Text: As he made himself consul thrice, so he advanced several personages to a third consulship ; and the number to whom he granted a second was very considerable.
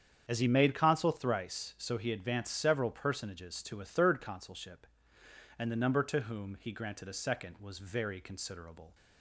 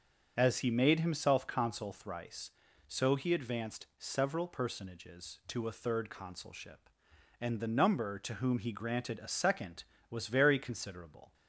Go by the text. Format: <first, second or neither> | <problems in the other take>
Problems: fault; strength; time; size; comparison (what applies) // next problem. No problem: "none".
second | starts louder than the rest; strong; until 1.2 s; 8 dB; also in the second // skips "himself"; at 0.7 s